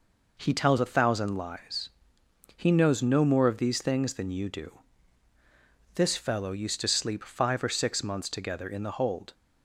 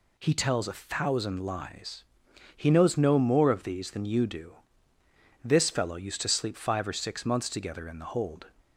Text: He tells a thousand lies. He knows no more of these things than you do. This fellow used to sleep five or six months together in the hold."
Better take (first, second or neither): first